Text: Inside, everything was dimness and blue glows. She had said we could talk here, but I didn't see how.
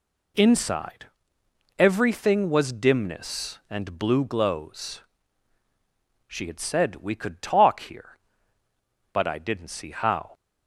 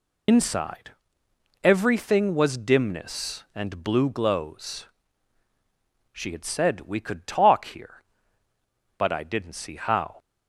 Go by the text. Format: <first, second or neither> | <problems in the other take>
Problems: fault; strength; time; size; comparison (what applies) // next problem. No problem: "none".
first | loses the start of "Inside"; at 0.2 s; 80 ms